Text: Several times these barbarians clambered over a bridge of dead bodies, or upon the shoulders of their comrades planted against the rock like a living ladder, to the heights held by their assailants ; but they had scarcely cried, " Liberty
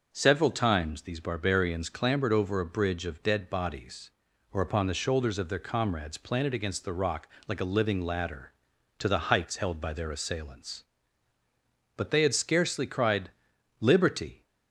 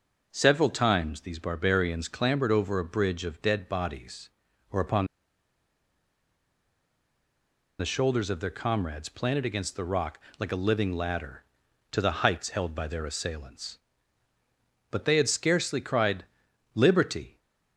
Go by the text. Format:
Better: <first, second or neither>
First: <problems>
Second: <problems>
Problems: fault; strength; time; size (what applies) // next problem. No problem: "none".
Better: first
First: pauses between "rock" and "like"; slight; at 7.2 s; 0.18 s long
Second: pauses between "upon" and "the"; strong; at 5.0 s; 2.7 s long // pauses between "rock" and "like"; slight; at 10.2 s; 0.18 s long